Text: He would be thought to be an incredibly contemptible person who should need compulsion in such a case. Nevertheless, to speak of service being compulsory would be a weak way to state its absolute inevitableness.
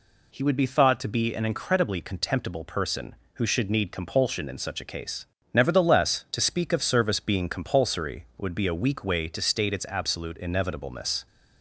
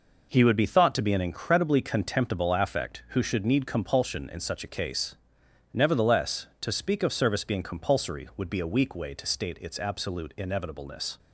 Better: first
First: none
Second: says "affect" for "person"; at 2.5 s

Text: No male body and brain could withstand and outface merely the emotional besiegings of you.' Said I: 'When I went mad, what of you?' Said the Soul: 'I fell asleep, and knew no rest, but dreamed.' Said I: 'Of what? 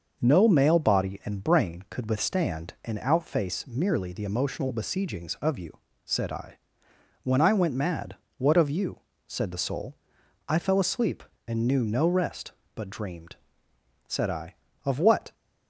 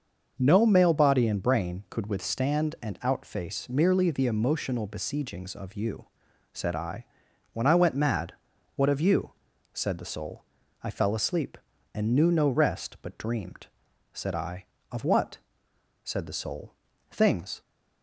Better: first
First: none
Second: starts louder than the rest; until 1.4 s; 6 dB // goes on to say "Said the Soul Things"; from 16.0 s on; 1.5 s long

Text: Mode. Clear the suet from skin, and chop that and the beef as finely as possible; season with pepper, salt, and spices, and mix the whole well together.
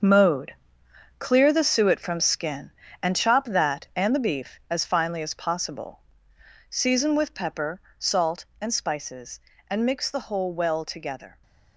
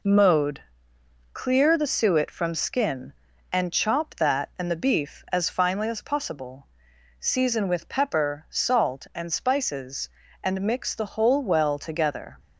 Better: second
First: gets quieter; strong; throughout; 10.5 dB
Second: none

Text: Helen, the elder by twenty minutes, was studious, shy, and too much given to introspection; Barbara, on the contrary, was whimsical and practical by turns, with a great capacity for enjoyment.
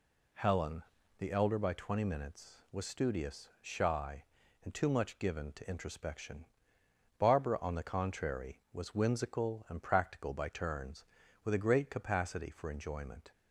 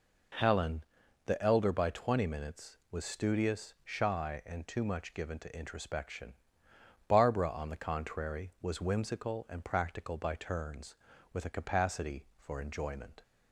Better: first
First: none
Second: skips "great"; at 11.5 s

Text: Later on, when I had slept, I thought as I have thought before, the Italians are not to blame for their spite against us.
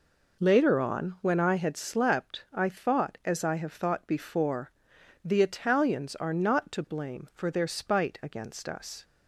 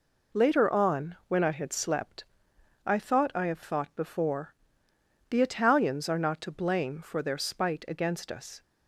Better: first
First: none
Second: skips "as"; at 3.3 s

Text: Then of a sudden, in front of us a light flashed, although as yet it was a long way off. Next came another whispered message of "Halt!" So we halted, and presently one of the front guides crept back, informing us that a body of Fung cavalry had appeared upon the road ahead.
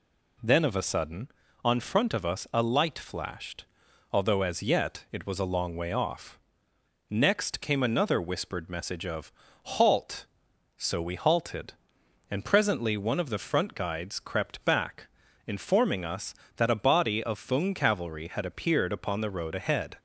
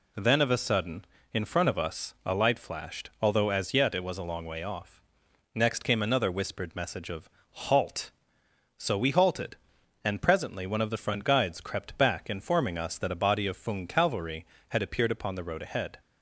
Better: second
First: says "on" for "in"; at 1.6 s // pauses between "of" and "Halt"; slight; at 9.3 s; 0.32 s long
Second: pauses between "of" and "Halt"; slight; at 7.2 s; 0.22 s long

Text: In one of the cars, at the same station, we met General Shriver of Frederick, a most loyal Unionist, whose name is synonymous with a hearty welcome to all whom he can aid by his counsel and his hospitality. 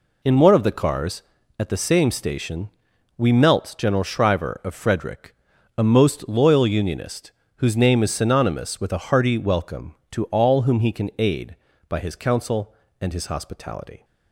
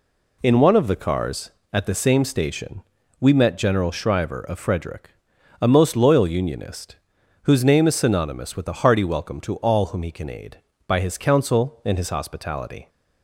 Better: second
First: says "melt" for "met"; at 3.3 s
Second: none

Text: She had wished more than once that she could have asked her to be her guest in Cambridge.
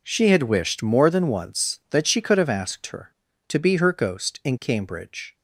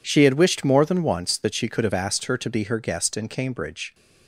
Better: second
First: says "ghost" for "guest"; at 3.9 s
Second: none

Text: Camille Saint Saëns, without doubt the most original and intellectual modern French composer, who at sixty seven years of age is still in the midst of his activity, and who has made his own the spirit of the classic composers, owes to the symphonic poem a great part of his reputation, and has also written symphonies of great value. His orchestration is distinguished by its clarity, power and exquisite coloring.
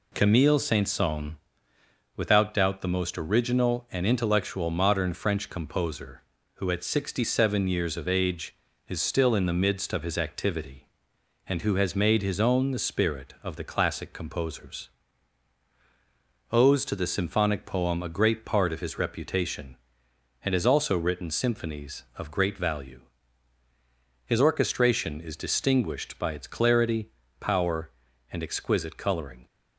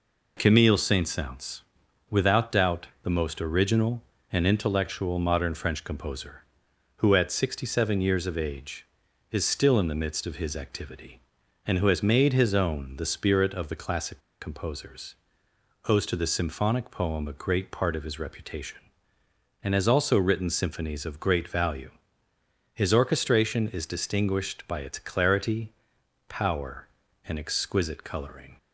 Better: first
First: none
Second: pauses between "doubt" and "the"; slight; at 2.8 s; 0.16 s long // pauses between "classic" and "composers"; slight; at 14.1 s; 0.21 s long

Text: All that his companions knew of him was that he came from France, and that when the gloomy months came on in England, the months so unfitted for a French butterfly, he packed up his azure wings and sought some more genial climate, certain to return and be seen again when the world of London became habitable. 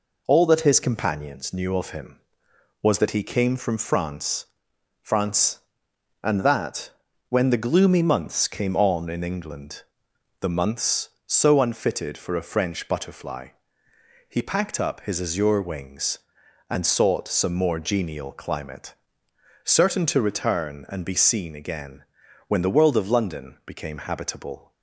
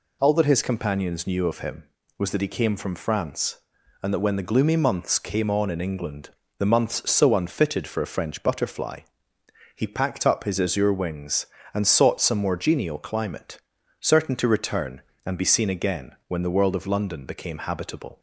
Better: second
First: says "France" twice; at 5.0 s // pauses between "that" and "when"; at 6.9 s; 0.38 s long // pauses between "again" and "when"; noticeable; at 22.0 s; 0.46 s long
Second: pauses between "again" and "when"; slight; at 16.1 s; 0.16 s long

